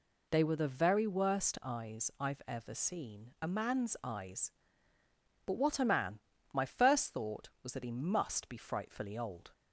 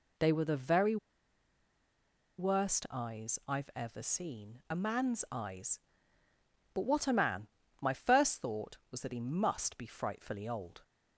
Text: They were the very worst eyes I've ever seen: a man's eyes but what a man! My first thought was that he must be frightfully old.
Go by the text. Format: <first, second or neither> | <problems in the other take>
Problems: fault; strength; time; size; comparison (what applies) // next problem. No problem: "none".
first | pauses between "very" and "worst"; strong; at 0.9 s; 1.4 s long